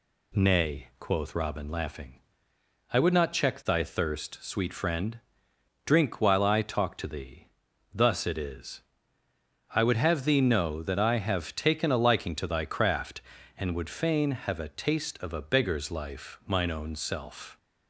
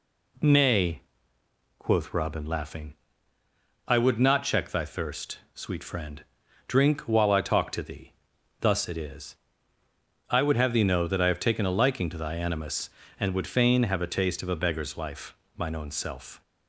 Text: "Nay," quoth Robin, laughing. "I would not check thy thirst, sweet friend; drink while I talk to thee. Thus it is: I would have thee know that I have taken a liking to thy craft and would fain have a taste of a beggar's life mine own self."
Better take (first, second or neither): first